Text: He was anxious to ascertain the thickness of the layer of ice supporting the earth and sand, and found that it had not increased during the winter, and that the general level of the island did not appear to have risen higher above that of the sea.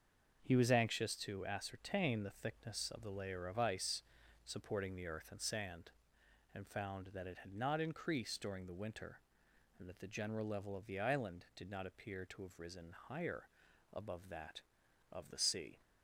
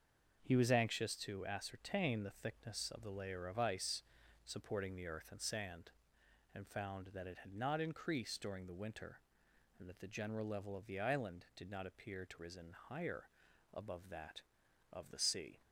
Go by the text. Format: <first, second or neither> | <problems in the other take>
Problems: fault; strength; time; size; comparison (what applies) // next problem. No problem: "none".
first | starts louder than the rest; until 1.4 s; 6.5 dB; also in the first // pauses between "ice" and "supporting"; at 4.0 s; 0.42 s long; also in the first // skips "have"; at 12.3 s // pauses between "higher" and "above"; at 13.2 s; 0.44 s long; also in the first